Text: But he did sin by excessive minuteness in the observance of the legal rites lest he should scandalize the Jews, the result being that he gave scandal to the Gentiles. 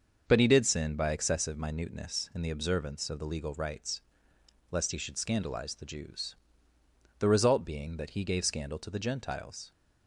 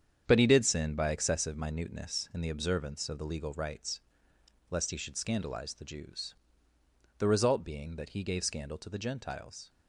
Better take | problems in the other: first | gets quieter; strong; throughout; 8.5 dB // starts louder than the rest; strong; until 1.2 s; 8 dB; also in the first // pauses between "rites" and "lest"; noticeable; at 4.0 s; 0.68 s long; noticeable in the first

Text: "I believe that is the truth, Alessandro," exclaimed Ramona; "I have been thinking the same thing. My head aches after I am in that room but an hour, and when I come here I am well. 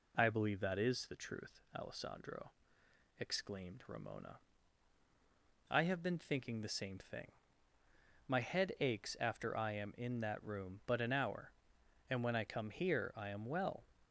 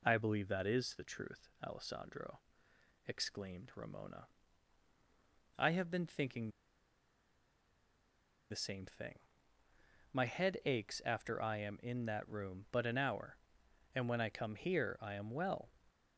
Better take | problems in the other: first | pauses between "thinking" and "the"; strong; at 6.4 s; 2.0 s long

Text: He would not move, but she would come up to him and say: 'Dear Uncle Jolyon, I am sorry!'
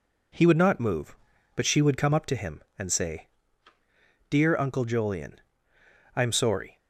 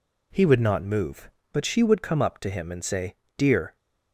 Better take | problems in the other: first | stops before "Uncle Jolyon I am sorry"; at 3.7 s

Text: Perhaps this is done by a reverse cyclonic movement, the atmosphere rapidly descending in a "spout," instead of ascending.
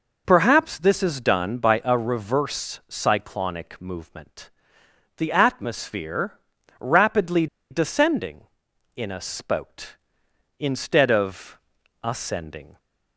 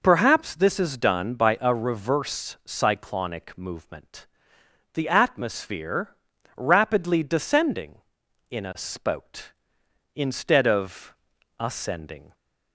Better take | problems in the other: second | pauses between "atmosphere" and "rapidly"; at 6.3 s; 0.40 s long; also in the second // pauses between "rapidly" and "descending"; slight; at 7.4 s; 0.24 s long // pauses between "of" and "ascending"; at 11.5 s; 0.44 s long; also in the second

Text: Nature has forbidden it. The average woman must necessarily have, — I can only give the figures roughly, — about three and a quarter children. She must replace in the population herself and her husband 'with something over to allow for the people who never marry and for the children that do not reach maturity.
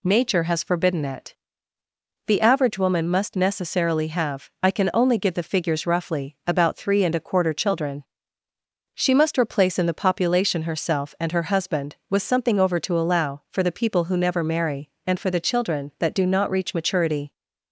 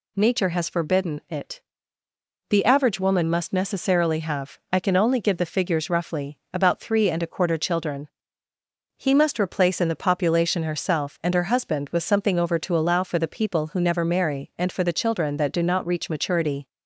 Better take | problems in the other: first | says "He" for "She"; at 8.9 s

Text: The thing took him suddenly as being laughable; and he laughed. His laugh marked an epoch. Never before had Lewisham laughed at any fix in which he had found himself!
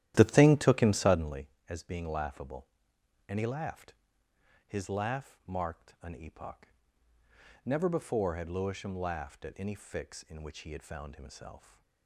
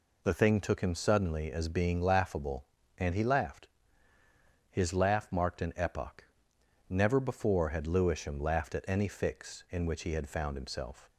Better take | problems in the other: second | starts louder than the rest; strong; until 1.4 s; 12.5 dB

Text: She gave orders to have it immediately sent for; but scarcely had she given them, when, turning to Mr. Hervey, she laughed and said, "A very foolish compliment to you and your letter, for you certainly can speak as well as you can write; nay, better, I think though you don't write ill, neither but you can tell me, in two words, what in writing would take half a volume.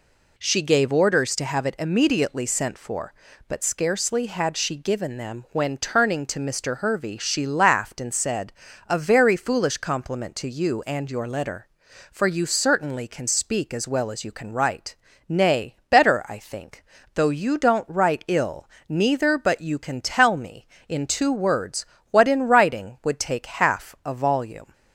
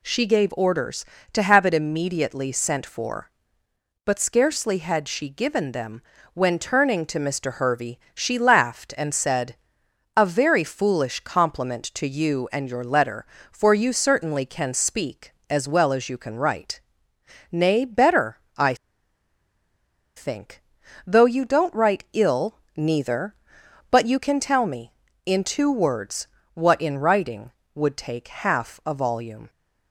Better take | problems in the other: first | pauses between "I" and "think"; strong; at 18.7 s; 1.4 s long // pauses between "think" and "though"; noticeable; at 20.6 s; 0.46 s long; slight in the first

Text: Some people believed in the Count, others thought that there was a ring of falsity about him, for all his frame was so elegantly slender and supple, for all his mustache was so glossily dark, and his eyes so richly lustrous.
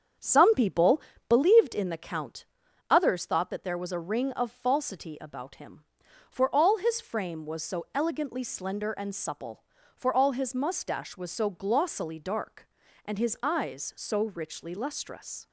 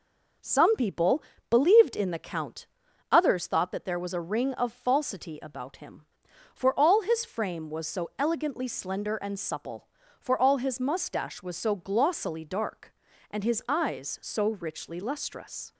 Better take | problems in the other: second | starts louder than the rest; strong; until 1.5 s; 7.5 dB // pauses between "people" and "believed"; slight; at 1.0 s; 0.28 s long; slight in the second

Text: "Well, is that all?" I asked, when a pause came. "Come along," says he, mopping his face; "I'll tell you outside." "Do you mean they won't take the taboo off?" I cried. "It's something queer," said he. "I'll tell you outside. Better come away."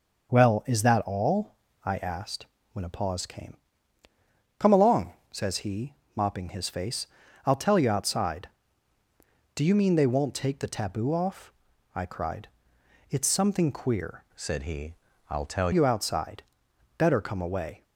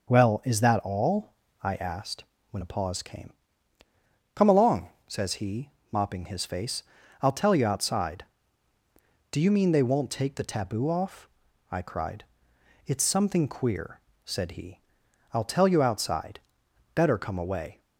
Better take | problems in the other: second | changes voice from "said" to "tell"; from 14.3 to 15.7 s; 1.4 s long

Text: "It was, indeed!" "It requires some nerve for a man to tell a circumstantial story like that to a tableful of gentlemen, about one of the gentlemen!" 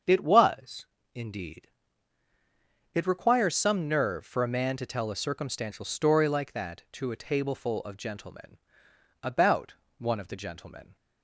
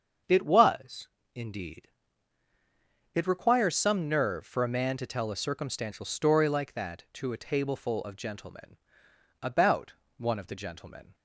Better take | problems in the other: neither | starts louder than the rest; the same in both // pauses between "about" and "one"; slight; the same in both

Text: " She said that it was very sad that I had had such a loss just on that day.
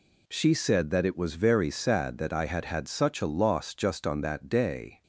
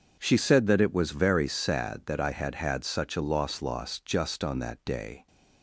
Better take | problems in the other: first | starts louder than the rest; until 1.1 s; 6.5 dB // says "loss" twice; at 3.6 s

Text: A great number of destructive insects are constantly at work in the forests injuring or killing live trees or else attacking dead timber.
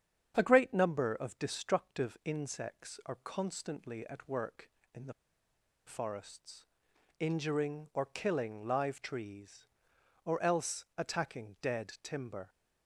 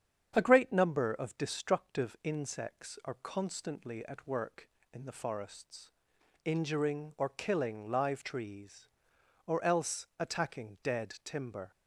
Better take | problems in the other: second | starts louder than the rest; strong; until 1.3 s; 8.5 dB; strong in the second // pauses between "the" and "forests"; noticeable; at 5.1 s; 0.73 s long // pauses between "forests" and "injuring"; noticeable; at 6.6 s; 0.54 s long; noticeable in the second

